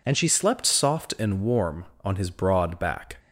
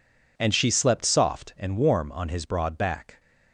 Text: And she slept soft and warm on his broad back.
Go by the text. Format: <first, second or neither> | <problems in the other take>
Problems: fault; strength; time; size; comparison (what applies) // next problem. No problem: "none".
second | changes voice at "slept"; from 0.2 s on; 2.9 s long